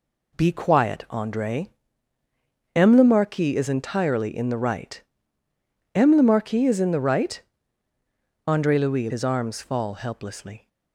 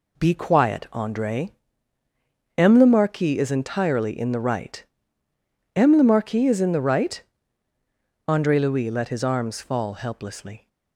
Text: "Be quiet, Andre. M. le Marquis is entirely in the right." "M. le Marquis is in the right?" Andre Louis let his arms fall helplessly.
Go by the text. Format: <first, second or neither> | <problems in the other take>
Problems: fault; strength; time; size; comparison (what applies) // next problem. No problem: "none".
second | skips "let"; at 9.1 s